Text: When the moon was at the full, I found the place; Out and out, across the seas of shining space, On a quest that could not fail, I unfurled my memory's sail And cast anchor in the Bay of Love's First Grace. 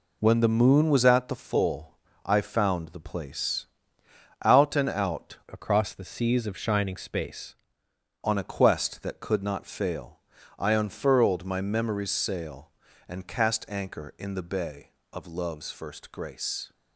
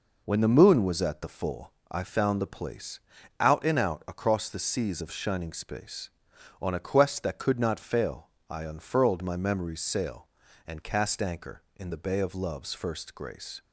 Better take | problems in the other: second | changes voice from "across" to "space"; from 5.4 to 7.5 s; 2.1 s long

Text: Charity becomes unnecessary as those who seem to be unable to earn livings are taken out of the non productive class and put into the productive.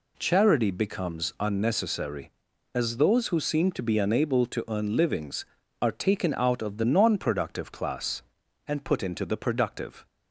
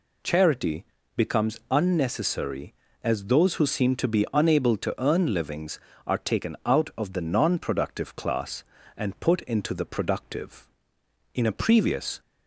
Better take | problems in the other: first | pauses between "Charity" and "becomes"; slight; at 0.8 s; 0.30 s long // goes on to say "In a previous"; noticeable; from 11.3 s on; 0.86 s long

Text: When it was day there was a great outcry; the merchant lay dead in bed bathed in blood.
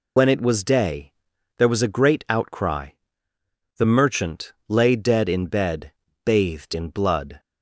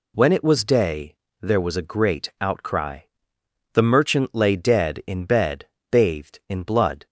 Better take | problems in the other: second | loses the start of "When"; at 0.1 s; 95 ms // pauses between "day" and "there"; at 1.1 s; 0.44 s long; slight in the second // pauses between "merchant" and "lay"; slight; at 4.5 s; 0.16 s long // pauses between "bed" and "bathed"; slight; at 5.9 s; 0.32 s long; slight in the second

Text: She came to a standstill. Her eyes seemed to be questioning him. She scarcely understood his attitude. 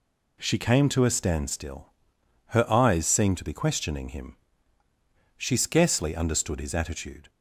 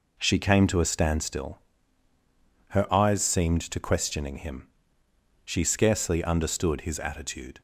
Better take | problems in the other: first | skips "be"; at 3.7 s

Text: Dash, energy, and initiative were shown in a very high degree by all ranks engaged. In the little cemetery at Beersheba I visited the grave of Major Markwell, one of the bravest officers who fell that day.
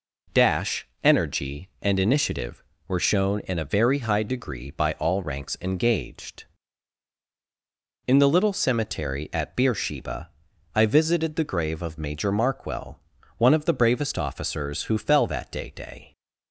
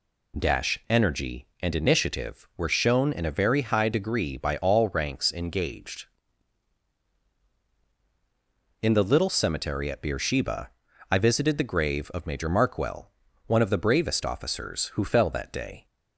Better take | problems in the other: second | pauses between "Beersheba" and "I"; at 10.2 s; 0.44 s long; also in the second // says "day" twice; at 15.7 s

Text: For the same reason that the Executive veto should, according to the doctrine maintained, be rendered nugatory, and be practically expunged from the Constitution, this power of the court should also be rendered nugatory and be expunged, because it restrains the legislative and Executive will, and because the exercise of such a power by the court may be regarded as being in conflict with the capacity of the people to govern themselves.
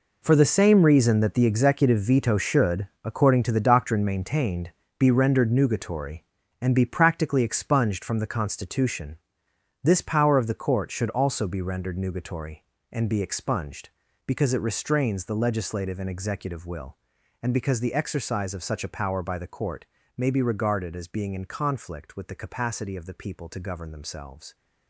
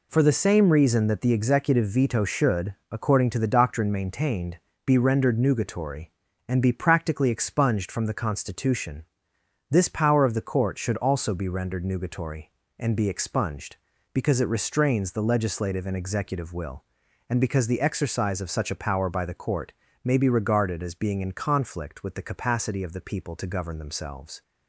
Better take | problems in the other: second | gets quieter; strong; throughout; 12.5 dB // pauses between "court" and "may"; slight; at 19.8 s; 0.30 s long; slight in the second

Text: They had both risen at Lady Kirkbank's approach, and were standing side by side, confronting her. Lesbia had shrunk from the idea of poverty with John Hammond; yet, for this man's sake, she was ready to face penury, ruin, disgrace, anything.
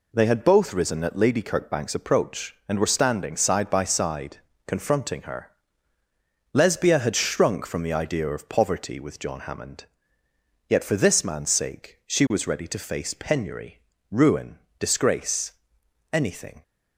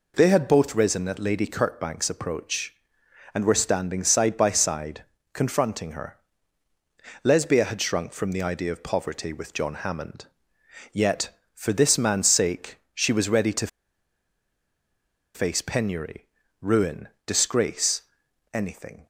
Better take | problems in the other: first | pauses between "to" and "face"; strong; at 13.6 s; 1.6 s long

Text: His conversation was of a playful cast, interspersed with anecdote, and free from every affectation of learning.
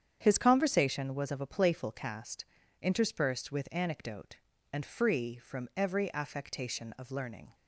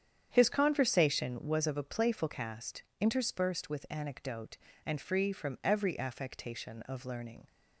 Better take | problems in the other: neither | starts louder than the rest; strong; the same in both

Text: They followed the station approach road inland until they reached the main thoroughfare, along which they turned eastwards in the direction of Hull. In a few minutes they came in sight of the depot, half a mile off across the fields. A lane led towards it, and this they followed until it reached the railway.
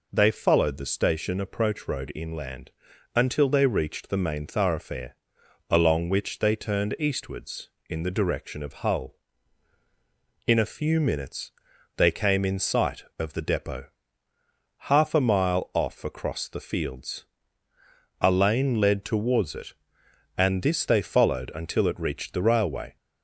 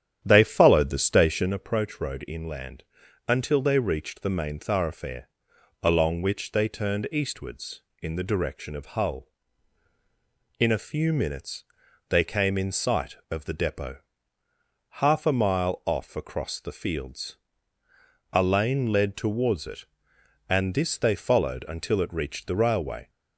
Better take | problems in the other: first | starts louder than the rest; strong; until 1.6 s; 10 dB // pauses between "inland" and "until"; at 2.8 s; 0.42 s long; also in the first // pauses between "minutes" and "they"; noticeable; at 11.6 s; 0.46 s long; noticeable in the first

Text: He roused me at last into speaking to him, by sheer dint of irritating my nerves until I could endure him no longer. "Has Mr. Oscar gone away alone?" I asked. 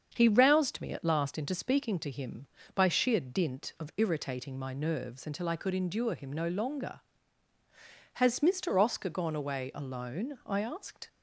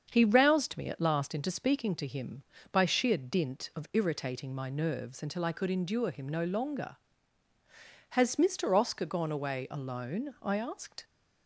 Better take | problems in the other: neither | starts louder than the rest; the same in both

